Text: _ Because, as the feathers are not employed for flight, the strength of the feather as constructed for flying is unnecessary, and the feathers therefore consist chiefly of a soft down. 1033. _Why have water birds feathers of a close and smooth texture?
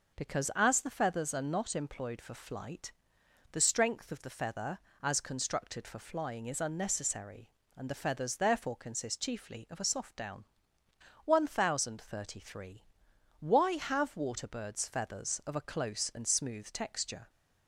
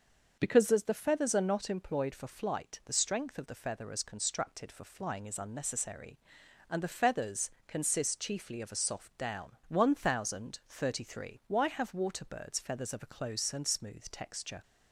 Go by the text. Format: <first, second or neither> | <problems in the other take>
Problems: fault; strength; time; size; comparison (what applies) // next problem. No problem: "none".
first | starts louder than the rest; until 1.4 s; 6.5 dB // skips "therefore"; at 7.5 s